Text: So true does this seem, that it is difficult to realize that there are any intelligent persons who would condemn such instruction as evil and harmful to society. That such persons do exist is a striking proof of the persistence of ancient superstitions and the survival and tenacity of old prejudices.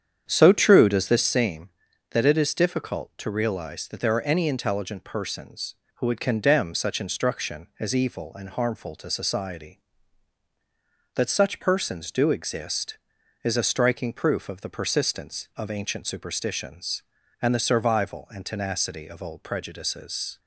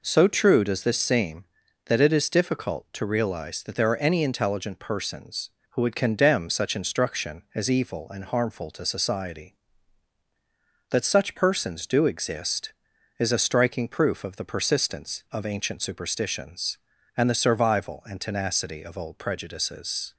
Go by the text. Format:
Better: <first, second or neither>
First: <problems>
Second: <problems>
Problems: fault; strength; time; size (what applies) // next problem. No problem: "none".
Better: second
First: starts louder than the rest; strong; until 1.4 s; 8.5 dB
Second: none